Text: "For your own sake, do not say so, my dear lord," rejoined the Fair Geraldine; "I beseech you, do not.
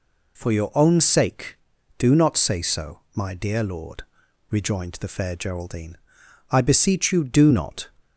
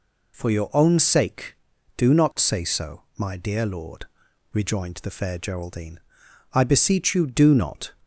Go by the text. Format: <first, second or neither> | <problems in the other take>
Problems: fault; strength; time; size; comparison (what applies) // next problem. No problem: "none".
neither | none